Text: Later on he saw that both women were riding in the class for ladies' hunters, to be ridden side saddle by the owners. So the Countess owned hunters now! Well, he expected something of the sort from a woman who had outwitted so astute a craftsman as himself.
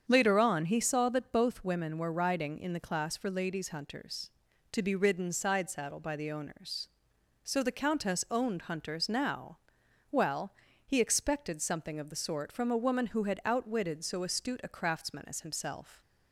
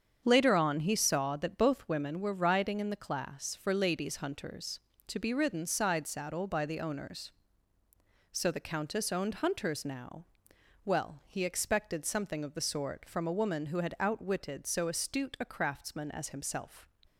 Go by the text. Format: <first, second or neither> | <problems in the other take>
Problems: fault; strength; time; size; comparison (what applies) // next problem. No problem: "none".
neither | starts louder than the rest; strong; the same in both